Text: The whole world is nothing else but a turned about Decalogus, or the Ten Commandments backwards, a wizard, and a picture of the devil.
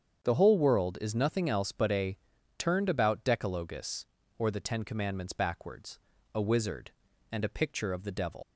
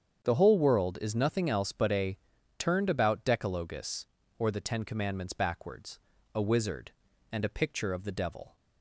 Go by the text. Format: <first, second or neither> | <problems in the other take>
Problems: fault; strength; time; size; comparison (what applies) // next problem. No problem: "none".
second | starts louder than the rest; strong; until 1.2 s; 7.5 dB; strong in the second // pauses between "a" and "turned"; at 2.1 s; 0.40 s long; also in the second // leaves "devil" unfinished; at 8.4 s; 130 ms